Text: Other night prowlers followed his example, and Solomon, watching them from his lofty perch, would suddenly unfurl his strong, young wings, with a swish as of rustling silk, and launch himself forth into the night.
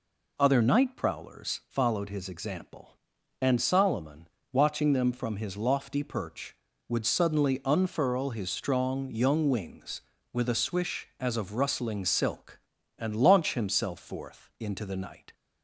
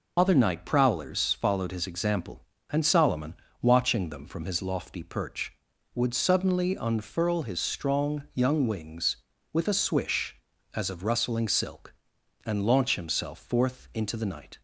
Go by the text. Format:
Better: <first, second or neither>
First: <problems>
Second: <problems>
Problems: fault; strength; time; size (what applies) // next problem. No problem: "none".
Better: first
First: none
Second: loses the start of "Other"; at 0.1 s; 80 ms